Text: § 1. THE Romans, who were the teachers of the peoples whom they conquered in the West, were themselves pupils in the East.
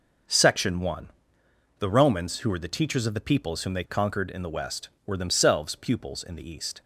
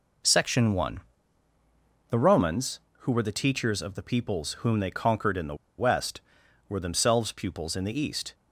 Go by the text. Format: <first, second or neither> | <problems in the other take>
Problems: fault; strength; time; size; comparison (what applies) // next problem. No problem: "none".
first | pauses between "the" and "West"; slight; at 5.5 s; 0.23 s long